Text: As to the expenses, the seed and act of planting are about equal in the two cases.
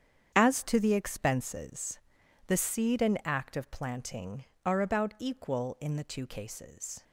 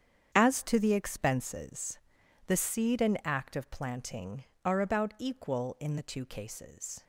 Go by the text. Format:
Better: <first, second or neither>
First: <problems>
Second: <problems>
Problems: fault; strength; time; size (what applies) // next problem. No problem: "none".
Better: neither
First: starts louder than the rest; strong; until 1.3 s; 8.5 dB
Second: starts louder than the rest; strong; until 1.3 s; 8.5 dB